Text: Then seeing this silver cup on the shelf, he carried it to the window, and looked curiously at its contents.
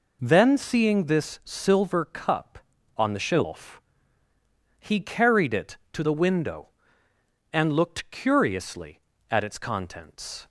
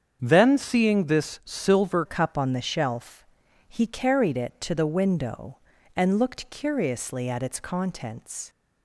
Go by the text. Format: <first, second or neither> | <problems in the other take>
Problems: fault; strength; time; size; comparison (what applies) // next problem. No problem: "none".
first | starts louder than the rest; strong; until 1.2 s; 7.5 dB // changes voice at "cup"; from 2.0 s on; 6.4 s long